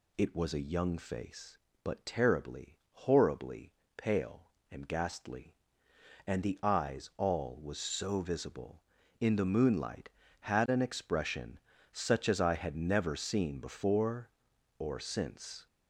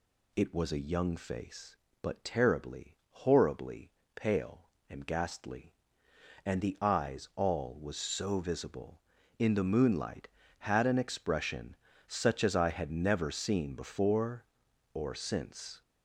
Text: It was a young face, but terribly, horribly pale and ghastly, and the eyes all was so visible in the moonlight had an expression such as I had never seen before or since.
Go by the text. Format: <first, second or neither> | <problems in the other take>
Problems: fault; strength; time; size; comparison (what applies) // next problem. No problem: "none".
neither | pauses between "horribly" and "pale"; slight; the same in both // pauses between "expression" and "such"; slight; the same in both